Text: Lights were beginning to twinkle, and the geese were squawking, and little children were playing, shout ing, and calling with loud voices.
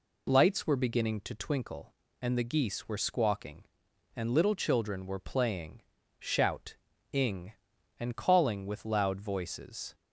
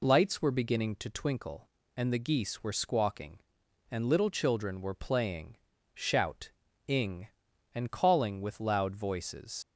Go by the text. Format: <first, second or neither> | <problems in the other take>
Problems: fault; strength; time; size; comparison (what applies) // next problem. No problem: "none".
first | pauses between "shout" and "ing"; at 6.5 s; 0.38 s long; also in the first // leaves "voices" unfinished; at 9.6 s; 65 ms